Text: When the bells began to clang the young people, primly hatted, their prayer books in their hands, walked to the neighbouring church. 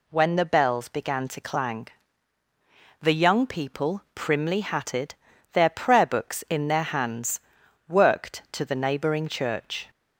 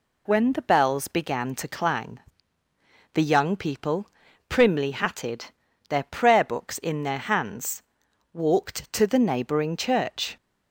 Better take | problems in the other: second | pauses between "clang" and "the"; at 1.8 s; 1.1 s long; noticeable in the second // says "worked" for "walked"; at 7.8 s

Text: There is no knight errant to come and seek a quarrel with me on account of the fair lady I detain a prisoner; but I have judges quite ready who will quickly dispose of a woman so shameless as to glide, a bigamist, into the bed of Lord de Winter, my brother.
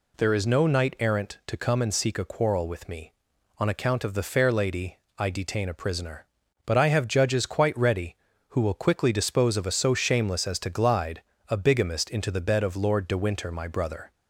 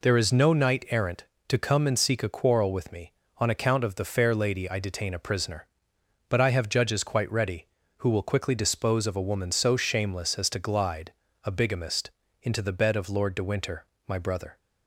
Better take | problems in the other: second | pauses between "lady" and "I"; slight; at 4.9 s; 0.20 s long // skips "woman"; at 9.7 s

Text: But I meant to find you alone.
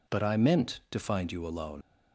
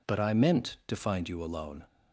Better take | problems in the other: second | leaves "alone" unfinished; at 1.8 s; 75 ms

